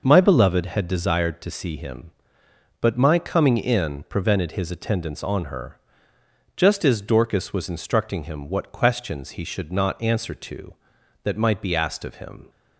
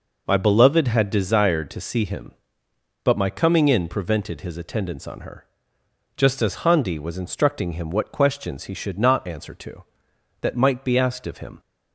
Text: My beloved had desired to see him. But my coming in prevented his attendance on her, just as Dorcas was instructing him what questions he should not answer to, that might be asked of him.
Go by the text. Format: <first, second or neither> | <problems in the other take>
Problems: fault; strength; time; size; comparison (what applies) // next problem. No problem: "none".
first | says "Handi" for "Dorcas"; at 6.5 s